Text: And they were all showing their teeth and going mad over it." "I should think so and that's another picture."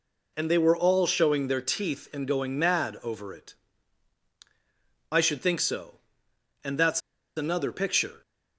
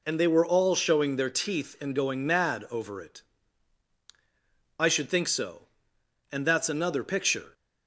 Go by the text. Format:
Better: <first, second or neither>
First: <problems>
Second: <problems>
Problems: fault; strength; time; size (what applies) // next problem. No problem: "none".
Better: second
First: pauses between "that's" and "another"; at 7.0 s; 0.36 s long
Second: none